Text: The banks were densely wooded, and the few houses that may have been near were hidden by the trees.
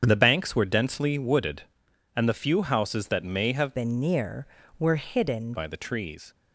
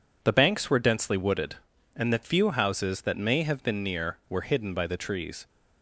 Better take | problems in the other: second | starts louder than the rest; strong; until 1.0 s; 7.5 dB // changes voice from "been" to "hidden"; from 3.7 to 5.5 s; 1.8 s long

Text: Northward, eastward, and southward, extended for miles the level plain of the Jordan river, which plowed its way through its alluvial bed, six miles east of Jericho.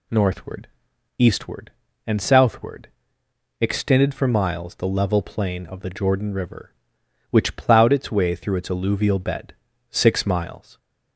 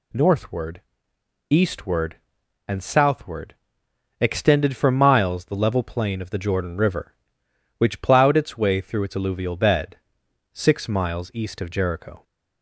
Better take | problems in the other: second | stops before "east of Jericho"; at 10.7 s

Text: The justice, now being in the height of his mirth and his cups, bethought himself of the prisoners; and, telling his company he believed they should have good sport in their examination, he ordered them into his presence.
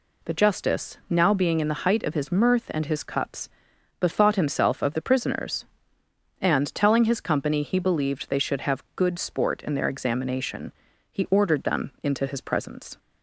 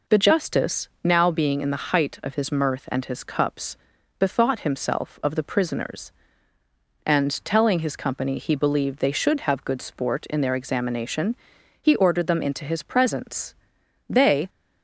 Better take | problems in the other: first | goes on to say "They"; slight; from 14.0 s on; 0.40 s long

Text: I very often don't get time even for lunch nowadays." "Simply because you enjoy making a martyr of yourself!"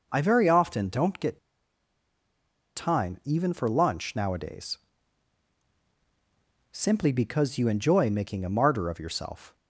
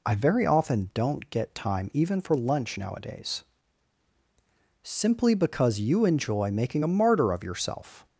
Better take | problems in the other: second | pauses between "get" and "time"; strong; at 1.3 s; 1.3 s long

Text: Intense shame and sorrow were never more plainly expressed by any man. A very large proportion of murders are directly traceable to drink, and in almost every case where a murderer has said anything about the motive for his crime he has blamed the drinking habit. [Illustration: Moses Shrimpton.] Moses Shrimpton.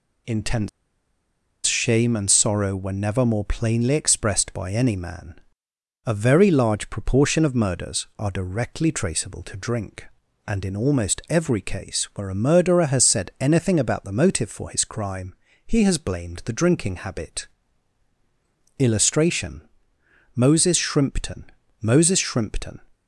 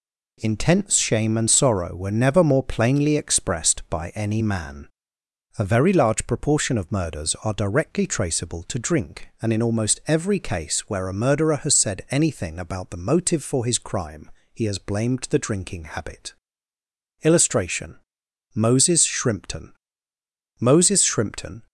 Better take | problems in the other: second | pauses between "Intense" and "shame"; noticeable; at 0.6 s; 0.97 s long // pauses between "crime" and "he"; slight; at 15.3 s; 0.32 s long; slight in the second

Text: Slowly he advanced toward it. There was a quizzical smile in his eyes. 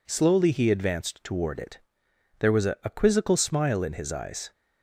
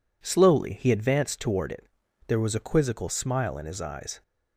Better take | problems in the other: second | says "a" twice; at 2.8 s

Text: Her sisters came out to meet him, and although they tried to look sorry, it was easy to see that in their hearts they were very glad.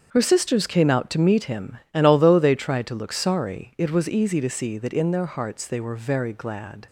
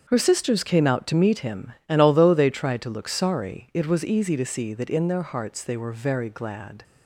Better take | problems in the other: neither | starts louder than the rest; the same in both

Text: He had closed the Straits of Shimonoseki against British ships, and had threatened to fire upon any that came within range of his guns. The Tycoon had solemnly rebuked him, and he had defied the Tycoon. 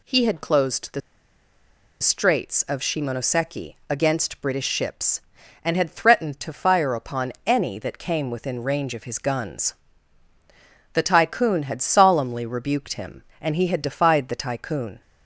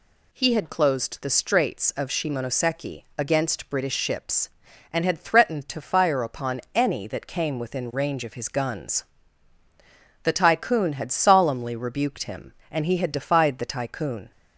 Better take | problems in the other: second | pauses between "the" and "Straits"; at 1.0 s; 1.0 s long

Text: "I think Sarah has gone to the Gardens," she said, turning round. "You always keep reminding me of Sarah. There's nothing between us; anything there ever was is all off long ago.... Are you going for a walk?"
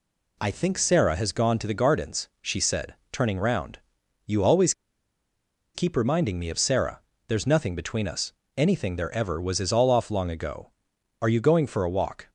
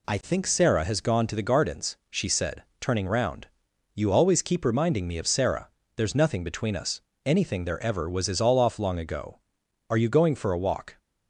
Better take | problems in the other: second | pauses between "always" and "keep"; at 4.7 s; 1.0 s long

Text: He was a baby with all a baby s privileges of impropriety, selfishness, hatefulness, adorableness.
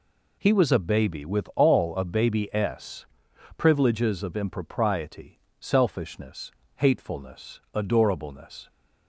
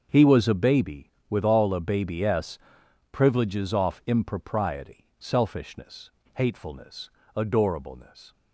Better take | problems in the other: first | starts louder than the rest; until 1.1 s; 6.5 dB // pauses between "s" and "privileges"; noticeable; at 2.5 s; 0.54 s long; noticeable in the first // says "off" for "of"; at 3.7 s

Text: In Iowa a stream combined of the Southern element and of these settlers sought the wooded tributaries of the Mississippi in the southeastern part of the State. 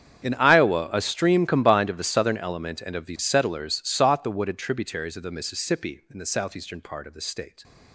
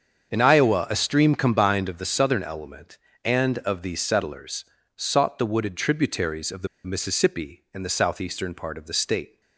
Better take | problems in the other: first | starts louder than the rest; until 1.3 s; 7 dB; strong in the first // pauses between "settlers" and "sought"; slight; at 4.6 s; 0.32 s long // pauses between "the" and "Mississippi"; slight; at 6.6 s; 0.18 s long

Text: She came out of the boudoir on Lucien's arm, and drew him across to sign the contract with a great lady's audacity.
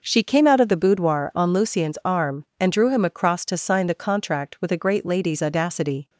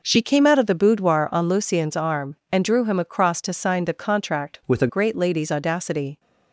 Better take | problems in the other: first | changes voice from "with" to "a"; from 4.6 to 4.8 s; 0.2 s long

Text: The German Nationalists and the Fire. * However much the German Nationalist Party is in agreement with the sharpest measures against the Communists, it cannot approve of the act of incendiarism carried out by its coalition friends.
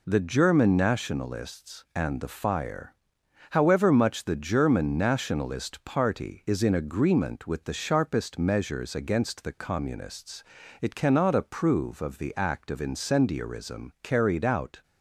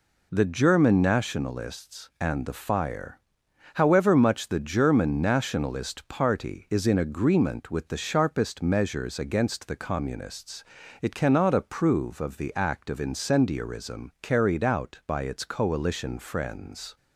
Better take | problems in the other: second | stops before "by its coalition friends"; at 14.8 s

